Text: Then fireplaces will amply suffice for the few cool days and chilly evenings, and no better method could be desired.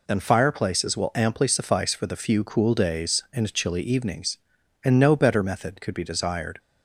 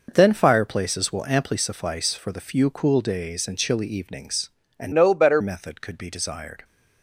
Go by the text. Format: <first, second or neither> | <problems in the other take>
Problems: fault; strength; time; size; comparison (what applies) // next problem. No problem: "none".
first | changes voice from "no" to "better"; from 4.9 to 5.4 s; 0.5 s long